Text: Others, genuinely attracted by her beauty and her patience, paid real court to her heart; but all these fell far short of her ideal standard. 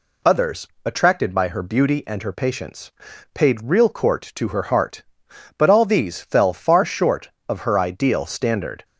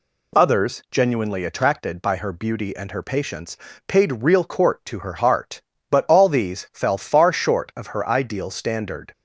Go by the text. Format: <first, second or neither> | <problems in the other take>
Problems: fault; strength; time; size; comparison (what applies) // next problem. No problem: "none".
second | skips "genuinely"; at 0.7 s